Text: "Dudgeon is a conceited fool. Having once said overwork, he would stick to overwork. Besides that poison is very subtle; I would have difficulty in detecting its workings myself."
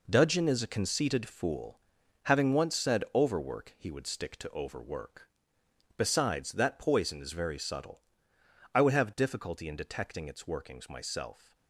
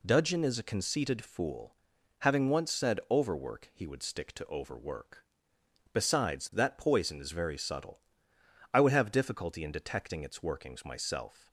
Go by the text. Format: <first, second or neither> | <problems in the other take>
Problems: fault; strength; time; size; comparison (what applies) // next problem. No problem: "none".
second | gets quieter; strong; throughout; 9 dB